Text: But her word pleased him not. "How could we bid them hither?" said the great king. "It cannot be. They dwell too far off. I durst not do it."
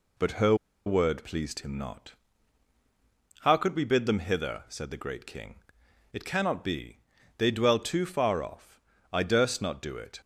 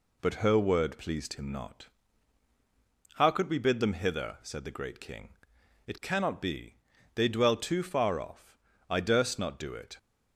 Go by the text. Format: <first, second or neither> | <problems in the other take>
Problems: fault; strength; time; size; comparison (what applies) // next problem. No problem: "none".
second | pauses between "her" and "word"; slight; at 0.5 s; 0.31 s long